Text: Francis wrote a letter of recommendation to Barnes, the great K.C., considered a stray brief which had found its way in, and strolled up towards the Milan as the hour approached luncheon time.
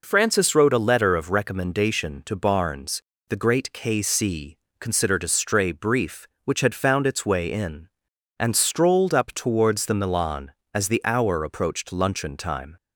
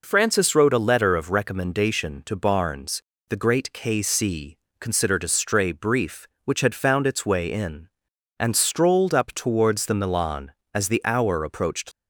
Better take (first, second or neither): first